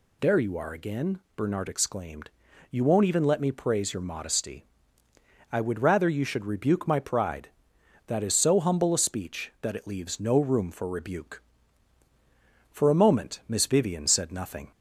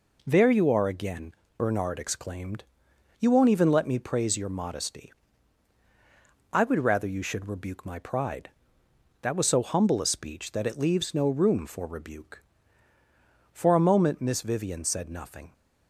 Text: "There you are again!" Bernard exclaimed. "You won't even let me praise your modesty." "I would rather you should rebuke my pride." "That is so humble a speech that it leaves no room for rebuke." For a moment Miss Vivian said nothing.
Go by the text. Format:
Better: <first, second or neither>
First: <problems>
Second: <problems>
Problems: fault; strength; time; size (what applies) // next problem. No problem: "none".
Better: first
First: none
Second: says "was" for "is"; at 9.3 s